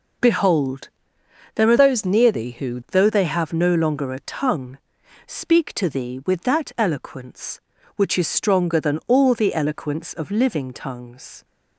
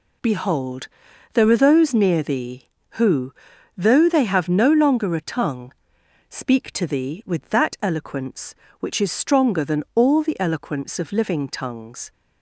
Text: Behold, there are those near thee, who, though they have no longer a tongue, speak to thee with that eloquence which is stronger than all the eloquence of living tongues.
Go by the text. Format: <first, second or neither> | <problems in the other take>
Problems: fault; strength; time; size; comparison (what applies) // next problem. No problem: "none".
second | changes voice from "those" to "who"; from 1.7 to 2.7 s; 1.0 s long